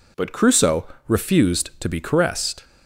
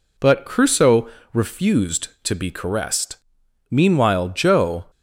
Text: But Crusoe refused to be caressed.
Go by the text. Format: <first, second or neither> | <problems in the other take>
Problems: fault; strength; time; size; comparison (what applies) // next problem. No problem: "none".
first | pauses between "Crusoe" and "refused"; slight; at 1.0 s; 0.26 s long; slight in the first // goes on to say "Meanwhile Joe"; noticeable; from 3.6 s on; 1.1 s long